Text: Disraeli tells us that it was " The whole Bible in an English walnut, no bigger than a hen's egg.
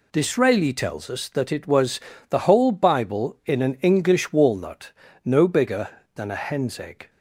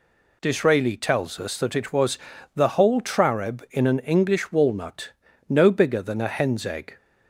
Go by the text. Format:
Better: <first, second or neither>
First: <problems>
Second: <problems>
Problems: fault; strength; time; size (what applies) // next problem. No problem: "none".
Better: first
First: none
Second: says "Trareb" for "Bible"; at 3.0 s